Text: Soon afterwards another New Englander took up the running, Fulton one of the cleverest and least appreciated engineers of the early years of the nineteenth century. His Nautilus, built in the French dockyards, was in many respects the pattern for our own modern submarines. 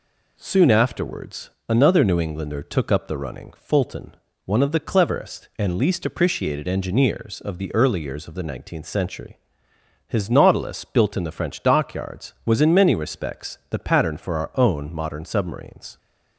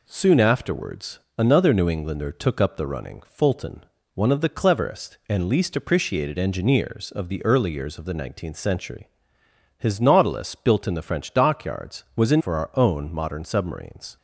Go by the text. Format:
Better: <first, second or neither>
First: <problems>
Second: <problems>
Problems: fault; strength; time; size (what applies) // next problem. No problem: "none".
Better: first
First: pauses between "afterwards" and "another"; slight; at 1.4 s; 0.18 s long // pauses between "Fulton" and "one"; slight; at 4.1 s; 0.30 s long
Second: pauses between "afterwards" and "another"; slight; at 1.1 s; 0.18 s long // pauses between "Fulton" and "one"; slight; at 3.8 s; 0.30 s long // skips "many respects the pattern"; at 12.4 s